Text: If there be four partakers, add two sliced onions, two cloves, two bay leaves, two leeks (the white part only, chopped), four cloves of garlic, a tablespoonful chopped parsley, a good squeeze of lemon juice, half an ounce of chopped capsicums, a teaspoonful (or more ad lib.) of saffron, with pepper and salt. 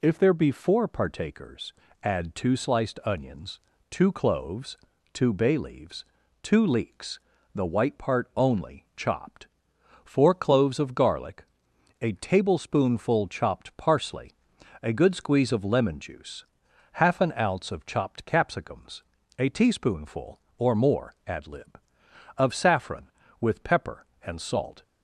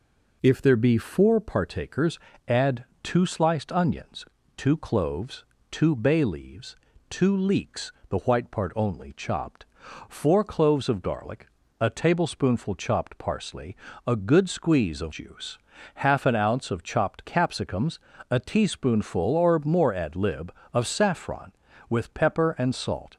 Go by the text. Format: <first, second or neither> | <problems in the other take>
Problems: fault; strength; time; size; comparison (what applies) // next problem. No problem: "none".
first | pauses between "add" and "two"; slight; at 2.8 s; 0.18 s long // skips "lemon"; at 15.1 s